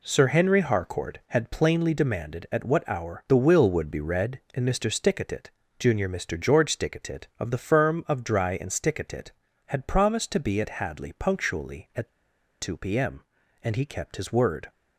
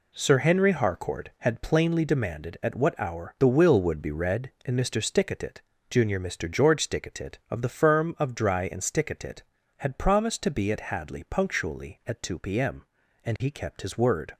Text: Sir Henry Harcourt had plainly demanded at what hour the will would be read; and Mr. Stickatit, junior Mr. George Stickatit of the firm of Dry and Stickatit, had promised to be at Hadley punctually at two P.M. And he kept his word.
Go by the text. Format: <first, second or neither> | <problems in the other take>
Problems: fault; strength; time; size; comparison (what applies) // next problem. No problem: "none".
second | pauses between "at" and "two"; noticeable; at 12.0 s; 0.49 s long